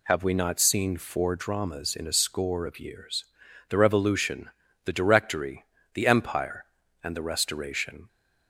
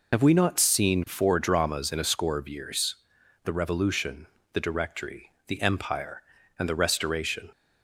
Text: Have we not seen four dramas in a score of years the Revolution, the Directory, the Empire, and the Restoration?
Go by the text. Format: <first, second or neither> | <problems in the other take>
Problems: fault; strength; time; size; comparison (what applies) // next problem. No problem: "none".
first | loses the start of "Have"; at 0.1 s; 75 ms // pauses between "years" and "the"; noticeable; at 2.9 s; 0.50 s long; noticeable in the first